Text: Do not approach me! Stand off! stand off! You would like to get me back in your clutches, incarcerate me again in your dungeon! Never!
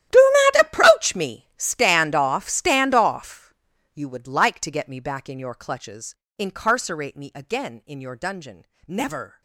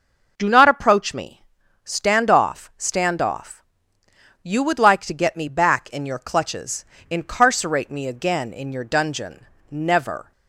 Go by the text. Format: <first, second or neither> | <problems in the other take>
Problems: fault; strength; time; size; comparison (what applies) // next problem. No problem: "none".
second | gets quieter; strong; throughout; 18.5 dB